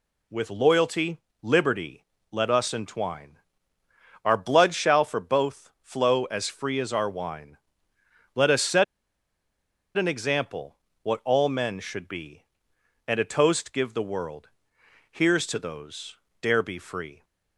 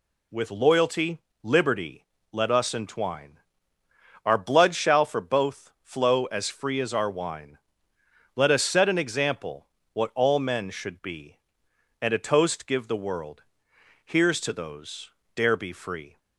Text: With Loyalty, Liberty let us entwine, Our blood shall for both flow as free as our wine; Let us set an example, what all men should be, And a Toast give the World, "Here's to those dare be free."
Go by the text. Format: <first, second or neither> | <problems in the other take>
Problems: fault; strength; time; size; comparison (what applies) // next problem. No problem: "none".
second | pauses between "Liberty" and "let"; slight; at 2.0 s; 0.28 s long; slight in the second // pauses between "set" and "an"; at 8.8 s; 1.1 s long // pauses between "those" and "dare"; slight; at 16.1 s; 0.24 s long; slight in the second